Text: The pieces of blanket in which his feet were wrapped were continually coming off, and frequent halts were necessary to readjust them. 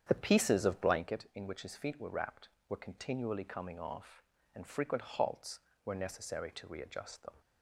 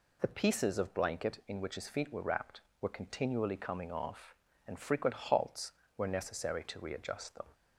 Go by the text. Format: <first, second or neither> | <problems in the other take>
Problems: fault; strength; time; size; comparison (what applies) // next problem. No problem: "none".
second | starts louder than the rest; strong; until 1.1 s; 8.5 dB